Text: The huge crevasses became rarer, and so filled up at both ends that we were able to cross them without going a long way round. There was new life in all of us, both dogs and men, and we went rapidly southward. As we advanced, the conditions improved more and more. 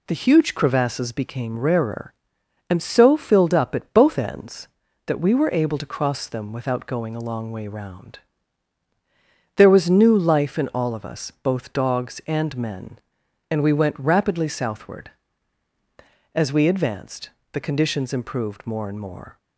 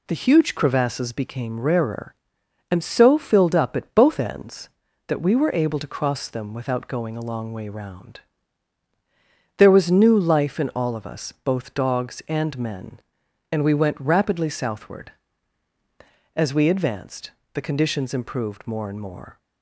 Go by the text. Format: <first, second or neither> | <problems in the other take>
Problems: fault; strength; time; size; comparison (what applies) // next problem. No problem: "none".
neither | none